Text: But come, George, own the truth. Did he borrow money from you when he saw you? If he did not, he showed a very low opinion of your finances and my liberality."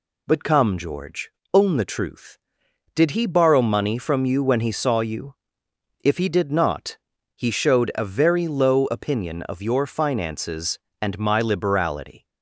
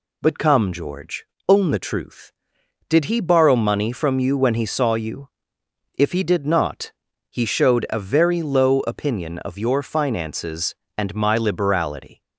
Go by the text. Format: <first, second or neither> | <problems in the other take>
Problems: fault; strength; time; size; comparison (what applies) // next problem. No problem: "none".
neither | none